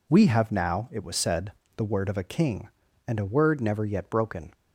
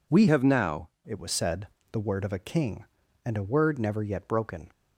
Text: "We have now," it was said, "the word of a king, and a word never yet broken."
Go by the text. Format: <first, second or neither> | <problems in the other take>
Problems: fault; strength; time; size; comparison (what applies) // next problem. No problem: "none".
first | changes voice from "have" to "now"; from 0.2 to 0.8 s; 0.6 s long